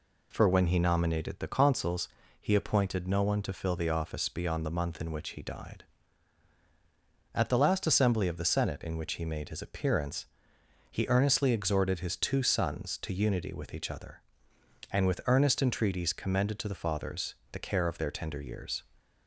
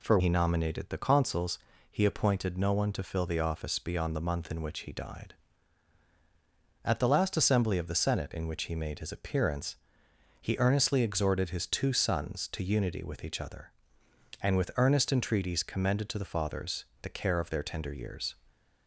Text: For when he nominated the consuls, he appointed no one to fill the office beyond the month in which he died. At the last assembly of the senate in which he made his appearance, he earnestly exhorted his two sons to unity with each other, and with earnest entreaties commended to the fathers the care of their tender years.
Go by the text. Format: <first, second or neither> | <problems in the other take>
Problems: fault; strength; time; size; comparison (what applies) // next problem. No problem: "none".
first | skips "when"; at 0.1 s // pauses between "fathers" and "the"; slight; at 16.8 s; 0.16 s long; slight in the first